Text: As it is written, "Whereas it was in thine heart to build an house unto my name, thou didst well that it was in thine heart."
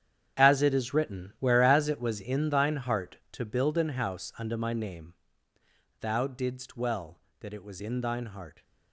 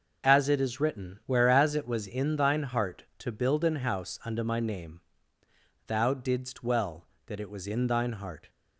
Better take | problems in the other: second | gets quieter; strong; throughout; 13 dB

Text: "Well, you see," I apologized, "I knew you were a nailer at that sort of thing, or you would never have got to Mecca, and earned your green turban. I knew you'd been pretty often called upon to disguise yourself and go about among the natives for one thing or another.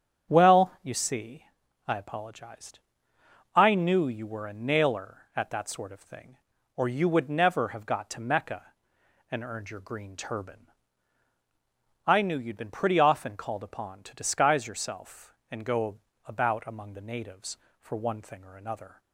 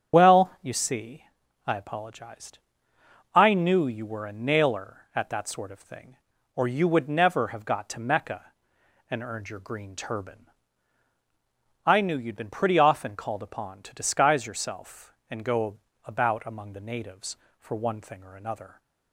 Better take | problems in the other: first | loses the start of "Well"; at 0.1 s; 40 ms // starts louder than the rest; strong; until 1.2 s; 8.5 dB; strong in the first // pauses between "go" and "about"; slight; at 15.7 s; 0.26 s long; slight in the first

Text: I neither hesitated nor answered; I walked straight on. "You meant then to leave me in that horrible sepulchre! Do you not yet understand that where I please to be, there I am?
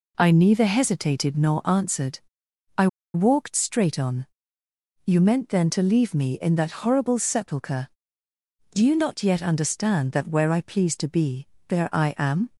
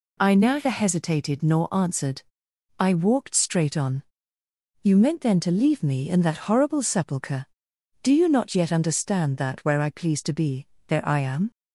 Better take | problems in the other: second | pauses between "I" and "walked"; slight; at 2.8 s; 0.27 s long

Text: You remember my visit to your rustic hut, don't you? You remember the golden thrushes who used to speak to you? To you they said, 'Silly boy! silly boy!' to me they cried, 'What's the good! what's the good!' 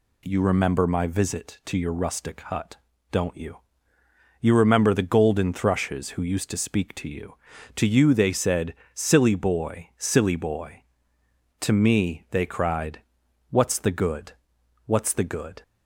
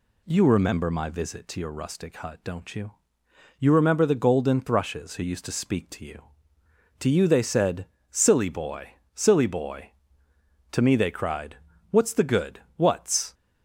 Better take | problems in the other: first | stops before "the good"; at 13.3 s

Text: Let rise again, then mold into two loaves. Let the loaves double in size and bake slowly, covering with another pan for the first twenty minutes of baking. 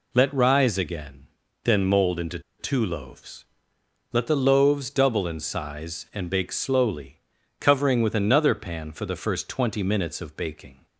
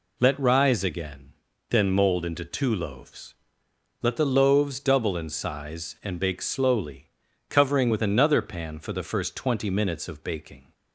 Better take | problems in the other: second | pauses between "into" and "two"; slight; at 2.3 s; 0.19 s long

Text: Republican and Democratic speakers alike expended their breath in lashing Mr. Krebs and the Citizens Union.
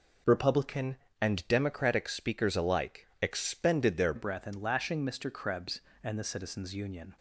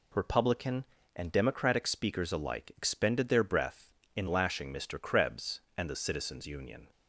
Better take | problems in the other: second | changes voice at "breath"; from 4.1 s on; 3.0 s long

